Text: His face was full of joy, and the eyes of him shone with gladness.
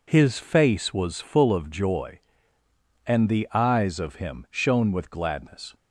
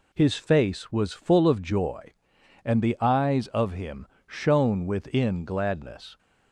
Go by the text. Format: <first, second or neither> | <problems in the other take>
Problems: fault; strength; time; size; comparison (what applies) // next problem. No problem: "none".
first | pauses between "him" and "shone"; slight; at 4.0 s; 0.20 s long // says "within" for "with"; at 4.8 s